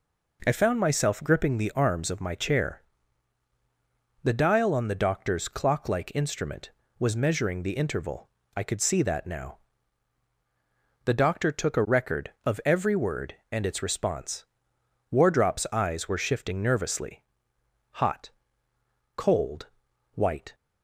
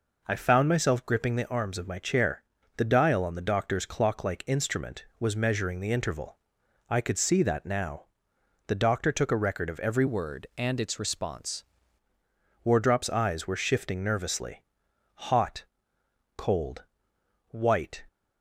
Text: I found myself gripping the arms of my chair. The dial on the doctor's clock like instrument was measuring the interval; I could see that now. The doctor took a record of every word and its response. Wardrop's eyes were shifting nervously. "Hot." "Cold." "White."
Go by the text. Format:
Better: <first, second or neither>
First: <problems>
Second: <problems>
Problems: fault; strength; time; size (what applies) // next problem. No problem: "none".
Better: first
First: none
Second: changes voice from "word" to "response"; from 10.0 to 11.6 s; 1.6 s long